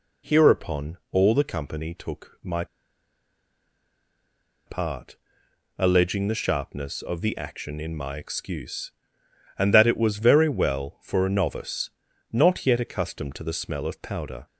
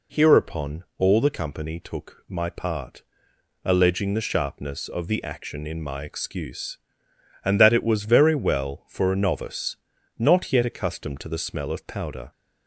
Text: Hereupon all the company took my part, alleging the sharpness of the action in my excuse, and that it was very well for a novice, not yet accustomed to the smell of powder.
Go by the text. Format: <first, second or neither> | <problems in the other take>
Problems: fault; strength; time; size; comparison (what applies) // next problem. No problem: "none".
second | pauses between "my" and "part"; strong; at 2.6 s; 2.0 s long